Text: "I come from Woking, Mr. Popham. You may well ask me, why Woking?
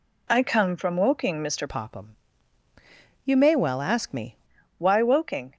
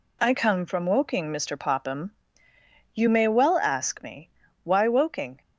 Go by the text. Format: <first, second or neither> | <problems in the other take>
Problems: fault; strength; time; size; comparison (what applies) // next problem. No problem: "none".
second | changes voice from "Popham" to "me"; from 1.6 to 4.3 s; 2.7 s long